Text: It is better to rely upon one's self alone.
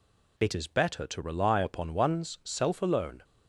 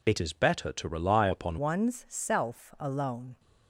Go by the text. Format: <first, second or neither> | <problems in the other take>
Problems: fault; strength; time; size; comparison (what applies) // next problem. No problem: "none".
first | changes voice at "one's"; from 1.5 s on; 1.8 s long